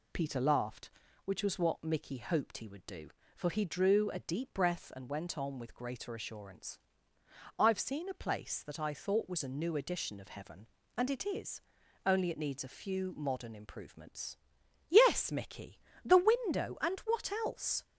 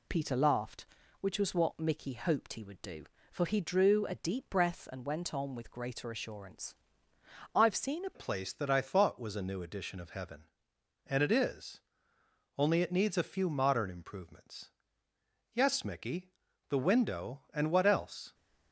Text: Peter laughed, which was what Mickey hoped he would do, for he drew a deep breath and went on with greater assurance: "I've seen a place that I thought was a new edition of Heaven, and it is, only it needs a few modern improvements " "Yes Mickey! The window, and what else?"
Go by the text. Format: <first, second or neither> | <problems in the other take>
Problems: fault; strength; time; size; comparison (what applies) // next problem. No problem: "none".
first | changes voice at "place"; from 8.1 s on; 10.2 s long